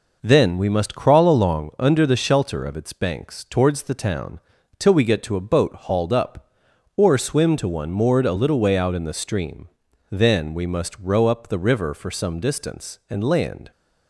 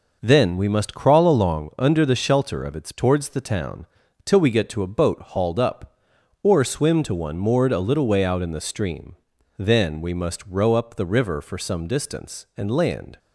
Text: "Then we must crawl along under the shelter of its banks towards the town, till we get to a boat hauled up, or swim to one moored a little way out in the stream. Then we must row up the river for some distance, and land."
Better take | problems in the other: first | skips "banks"; at 2.9 s

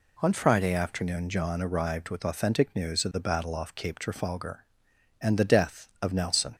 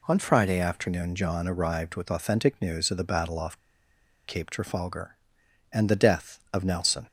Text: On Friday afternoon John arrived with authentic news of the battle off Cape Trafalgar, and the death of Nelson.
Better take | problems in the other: first | pauses between "off" and "Cape"; noticeable; at 3.5 s; 0.69 s long

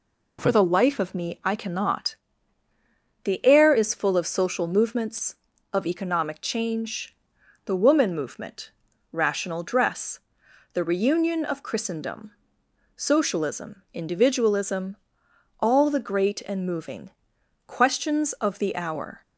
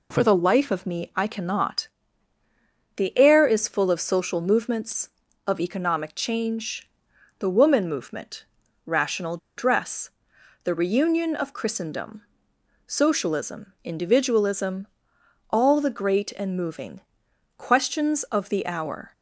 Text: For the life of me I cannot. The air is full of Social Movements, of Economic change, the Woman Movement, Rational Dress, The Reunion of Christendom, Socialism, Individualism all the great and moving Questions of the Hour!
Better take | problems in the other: first | pauses between "Rational" and "Dress"; slight; at 9.3 s; 0.19 s long // pauses between "Individualism" and "all"; noticeable; at 14.8 s; 0.64 s long; noticeable in the first // pauses between "moving" and "Questions"; noticeable; at 17.0 s; 0.56 s long; noticeable in the first

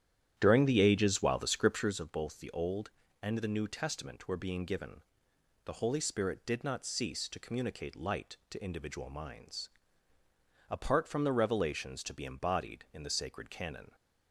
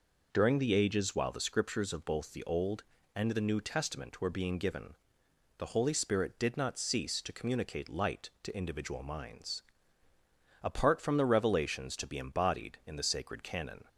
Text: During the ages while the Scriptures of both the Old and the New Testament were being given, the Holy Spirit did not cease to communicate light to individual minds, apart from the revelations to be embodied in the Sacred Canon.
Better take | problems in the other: second | starts louder than the rest; strong; until 2.0 s; 10.5 dB

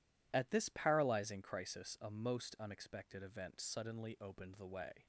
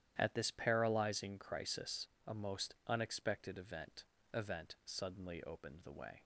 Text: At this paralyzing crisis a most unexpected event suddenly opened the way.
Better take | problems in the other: first | starts louder than the rest; strong; until 1.1 s; 11 dB // pauses between "crisis" and "a"; slight; at 2.0 s; 0.20 s long // says "event" twice; at 4.3 s

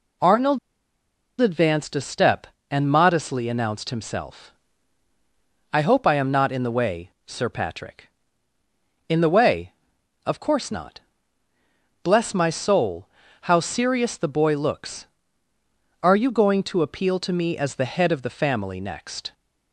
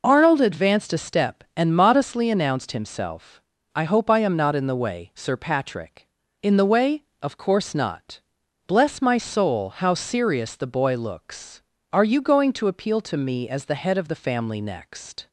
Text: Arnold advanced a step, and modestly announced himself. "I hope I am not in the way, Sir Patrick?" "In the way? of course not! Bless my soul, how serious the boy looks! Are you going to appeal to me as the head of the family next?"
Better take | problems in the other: second | pauses between "Arnold" and "advanced"; noticeable; at 0.5 s; 0.82 s long

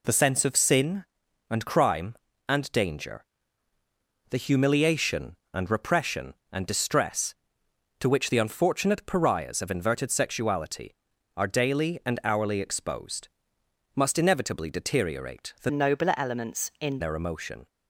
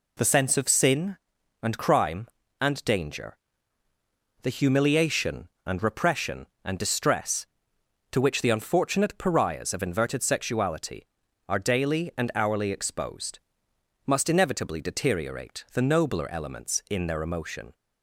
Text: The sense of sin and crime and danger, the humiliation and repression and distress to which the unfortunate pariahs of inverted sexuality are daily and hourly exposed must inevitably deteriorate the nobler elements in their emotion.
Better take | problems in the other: second | pauses between "exposed" and "must"; noticeable; at 13.2 s; 0.66 s long; noticeable in the second // changes voice from "nobler" to "in"; from 15.7 to 17.0 s; 1.3 s long

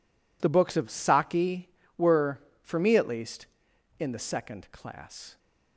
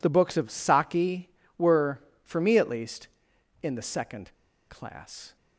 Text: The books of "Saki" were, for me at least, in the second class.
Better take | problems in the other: first | pauses between "second" and "class"; slight; at 4.3 s; 0.35 s long

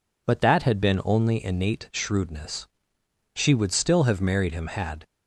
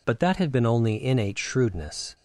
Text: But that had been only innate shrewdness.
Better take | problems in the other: second | goes on to say "She would still have married him had"; strong; from 3.3 s on; 1.7 s long

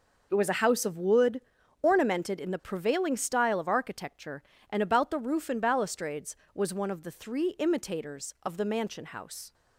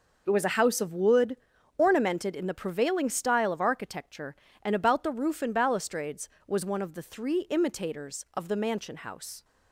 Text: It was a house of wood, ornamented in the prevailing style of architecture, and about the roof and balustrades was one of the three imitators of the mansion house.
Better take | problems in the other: neither | none

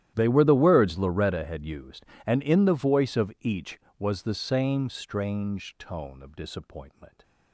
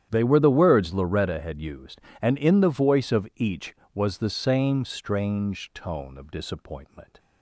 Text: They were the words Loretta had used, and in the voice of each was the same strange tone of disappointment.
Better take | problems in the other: second | gets quieter; strong; throughout; 22.5 dB // starts louder than the rest; strong; until 1.1 s; 12 dB; strong in the second

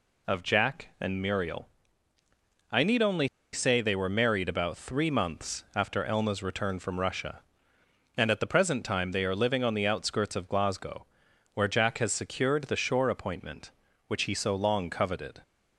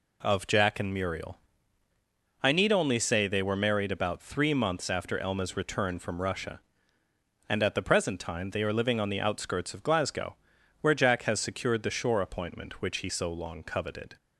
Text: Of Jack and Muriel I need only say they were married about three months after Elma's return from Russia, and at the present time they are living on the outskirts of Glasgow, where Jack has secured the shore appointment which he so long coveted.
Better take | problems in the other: second | pauses between "Muriel" and "I"; at 1.6 s; 1.0 s long; also in the second // pauses between "only" and "say"; slight; at 3.2 s; 0.24 s long

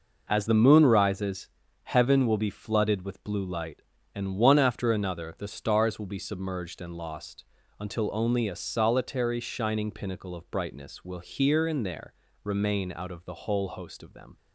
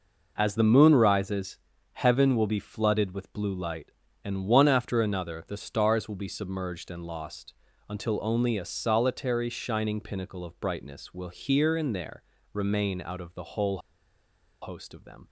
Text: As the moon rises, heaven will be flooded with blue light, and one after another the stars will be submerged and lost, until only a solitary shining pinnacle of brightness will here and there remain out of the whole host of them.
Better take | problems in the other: first | pauses between "there" and "remain"; slight; at 12.2 s; 0.32 s long; slight in the first // pauses between "whole" and "host"; noticeable; at 13.7 s; 0.83 s long

